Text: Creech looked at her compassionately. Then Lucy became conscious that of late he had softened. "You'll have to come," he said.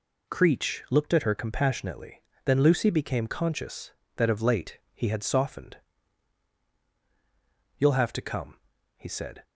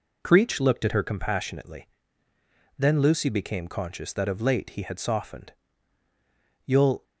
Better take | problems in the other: first | stops before "have to come he said"; at 7.0 s

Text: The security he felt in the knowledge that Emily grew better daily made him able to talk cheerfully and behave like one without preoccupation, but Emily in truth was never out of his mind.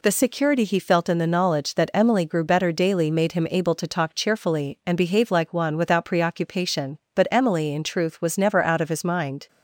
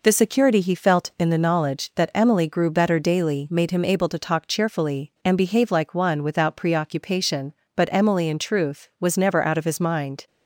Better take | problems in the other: neither | none

